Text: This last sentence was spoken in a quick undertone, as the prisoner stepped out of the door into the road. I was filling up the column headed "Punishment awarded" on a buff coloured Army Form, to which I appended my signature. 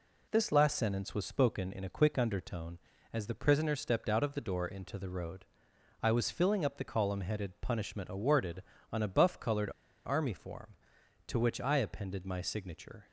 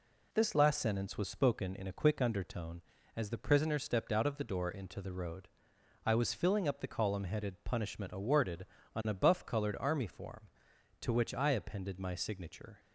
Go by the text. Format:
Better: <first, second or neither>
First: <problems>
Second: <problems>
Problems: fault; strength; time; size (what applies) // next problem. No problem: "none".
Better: second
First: pauses between "coloured" and "Army"; slight; at 9.6 s; 0.35 s long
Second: none